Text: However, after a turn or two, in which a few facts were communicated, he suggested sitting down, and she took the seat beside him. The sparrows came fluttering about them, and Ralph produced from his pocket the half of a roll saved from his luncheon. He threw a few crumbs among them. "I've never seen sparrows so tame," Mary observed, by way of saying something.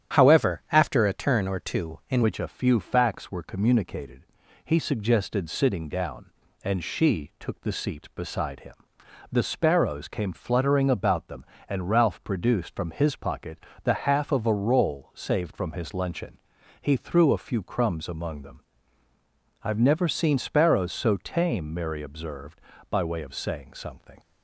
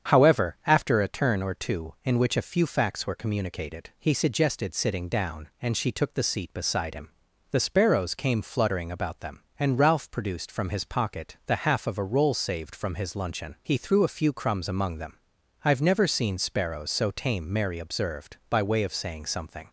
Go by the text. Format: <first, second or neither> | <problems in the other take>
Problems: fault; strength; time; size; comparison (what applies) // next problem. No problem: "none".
second | starts louder than the rest; strong; until 1.2 s; 9 dB; strong in the second // changes voice at "which"; from 2.2 s on; 21.9 s long // pauses between "pocket" and "the"; slight; at 13.5 s; 0.26 s long